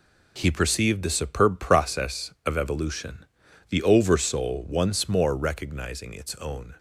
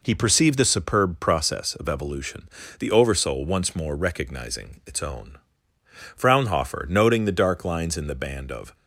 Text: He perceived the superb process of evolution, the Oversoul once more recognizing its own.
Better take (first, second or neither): first